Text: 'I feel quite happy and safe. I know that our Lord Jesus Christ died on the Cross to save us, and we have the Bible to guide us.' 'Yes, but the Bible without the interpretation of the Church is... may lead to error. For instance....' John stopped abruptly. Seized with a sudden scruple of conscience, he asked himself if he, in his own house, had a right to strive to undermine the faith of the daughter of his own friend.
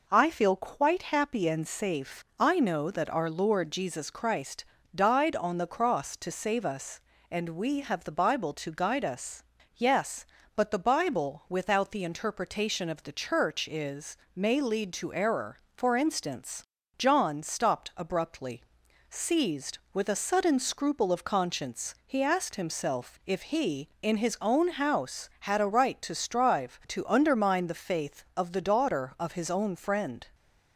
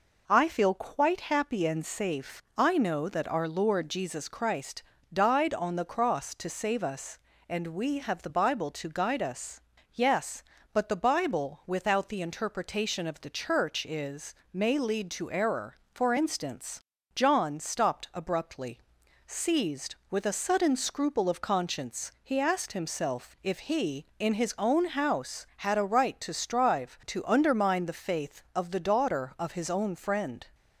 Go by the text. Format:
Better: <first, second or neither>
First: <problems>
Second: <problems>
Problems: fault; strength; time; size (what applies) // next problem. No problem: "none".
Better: neither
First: pauses between "Christ" and "died"; slight; at 4.6 s; 0.32 s long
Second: pauses between "Christ" and "died"; slight; at 4.8 s; 0.32 s long